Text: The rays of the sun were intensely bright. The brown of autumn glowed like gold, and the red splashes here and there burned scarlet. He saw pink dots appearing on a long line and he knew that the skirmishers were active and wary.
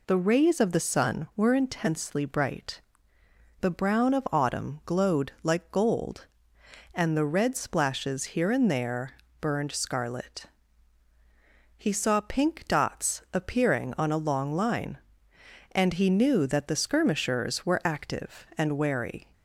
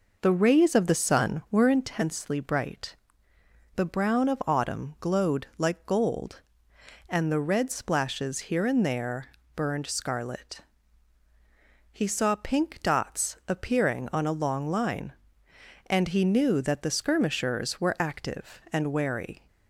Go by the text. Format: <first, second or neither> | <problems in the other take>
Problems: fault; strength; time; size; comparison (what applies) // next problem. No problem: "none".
first | starts louder than the rest; noticeable; until 1.9 s; 5 dB // pauses between "there" and "burned"; slight; at 9.2 s; 0.26 s long; slight in the first